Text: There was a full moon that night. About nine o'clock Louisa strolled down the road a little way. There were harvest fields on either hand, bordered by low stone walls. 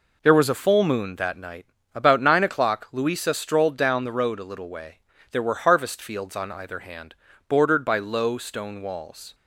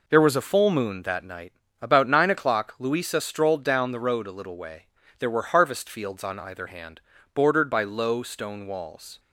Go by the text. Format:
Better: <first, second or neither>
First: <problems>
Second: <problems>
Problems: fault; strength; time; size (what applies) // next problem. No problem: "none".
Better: neither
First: none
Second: none